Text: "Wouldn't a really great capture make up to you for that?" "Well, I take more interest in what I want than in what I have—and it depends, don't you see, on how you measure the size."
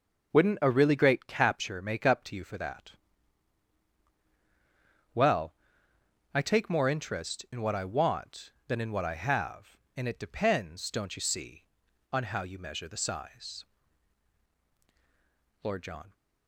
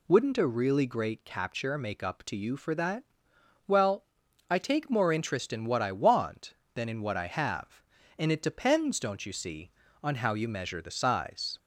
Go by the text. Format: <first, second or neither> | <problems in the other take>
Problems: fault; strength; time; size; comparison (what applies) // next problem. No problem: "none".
second | goes on to say "Lord John"; from 15.6 s on; 0.50 s long